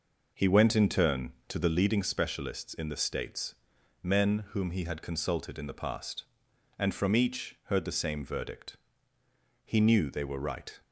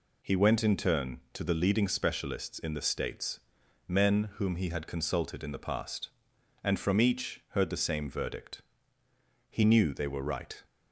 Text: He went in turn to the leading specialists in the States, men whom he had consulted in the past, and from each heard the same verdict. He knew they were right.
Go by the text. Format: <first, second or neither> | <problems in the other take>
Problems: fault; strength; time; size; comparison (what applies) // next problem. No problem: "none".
second | starts louder than the rest; noticeable; until 2.0 s; 5.5 dB